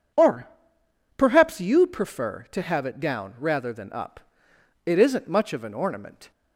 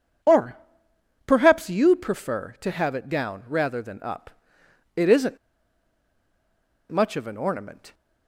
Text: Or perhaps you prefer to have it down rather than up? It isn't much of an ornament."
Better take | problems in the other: first | pauses between "Or" and "perhaps"; noticeable; at 0.5 s; 0.70 s long; noticeable in the first // pauses between "isn't" and "much"; strong; at 5.3 s; 1.5 s long

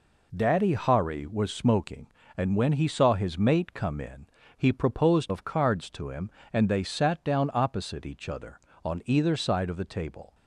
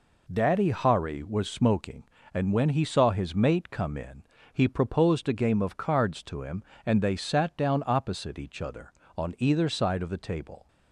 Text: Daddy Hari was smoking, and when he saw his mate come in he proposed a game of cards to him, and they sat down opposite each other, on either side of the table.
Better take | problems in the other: second | pauses between "in" and "he"; slight; at 4.2 s; 0.30 s long; slight in the second // skips "a game"; at 5.3 s

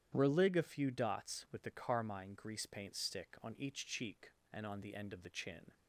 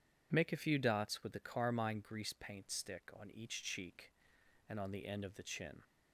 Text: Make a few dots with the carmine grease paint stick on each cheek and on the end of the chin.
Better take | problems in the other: second | starts louder than the rest; strong; until 1.1 s; 10 dB // says "Relig" for "Make"; at 0.1 s

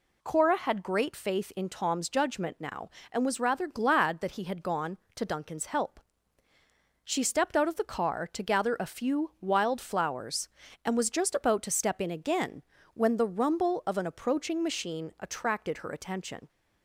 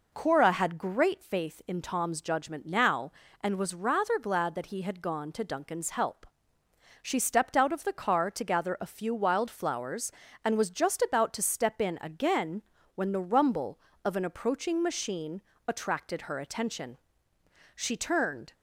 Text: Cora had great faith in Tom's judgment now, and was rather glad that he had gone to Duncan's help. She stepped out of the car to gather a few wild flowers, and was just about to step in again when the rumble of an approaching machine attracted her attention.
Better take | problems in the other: first | pauses between "again" and "when"; slight; at 12.6 s; 0.34 s long; slight in the first // pauses between "machine" and "attracted"; slight; at 15.4 s; 0.26 s long // goes on to say "She turned"; noticeable; from 17.7 s on; 0.78 s long

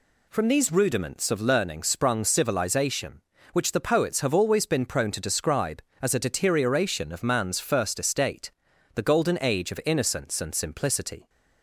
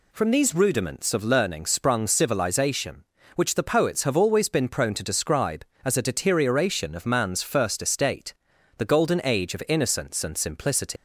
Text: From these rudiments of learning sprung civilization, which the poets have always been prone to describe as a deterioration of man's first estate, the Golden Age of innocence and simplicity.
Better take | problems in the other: first | leaves "simplicity" unfinished; at 10.9 s; 160 ms

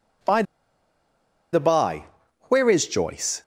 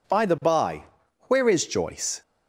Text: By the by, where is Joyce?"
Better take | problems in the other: second | pauses between "By" and "the"; at 0.4 s; 1.0 s long

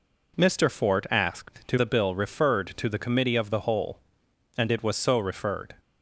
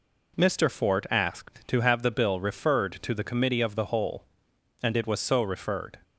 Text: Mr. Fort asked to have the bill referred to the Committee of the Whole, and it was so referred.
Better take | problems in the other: second | skips "have"; at 1.7 s

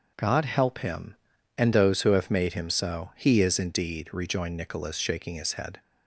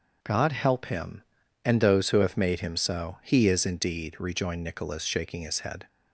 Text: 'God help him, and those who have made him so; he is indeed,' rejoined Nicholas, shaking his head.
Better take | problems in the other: neither | none

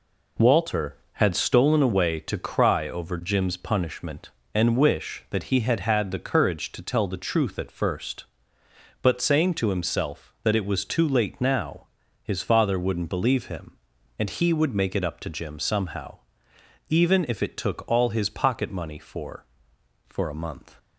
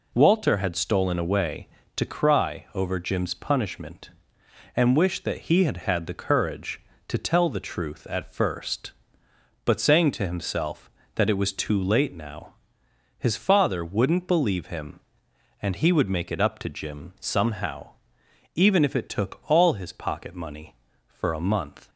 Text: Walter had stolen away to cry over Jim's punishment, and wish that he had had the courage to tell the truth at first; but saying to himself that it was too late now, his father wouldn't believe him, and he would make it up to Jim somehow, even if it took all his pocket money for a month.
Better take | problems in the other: second | says "for" twice; at 20.0 s

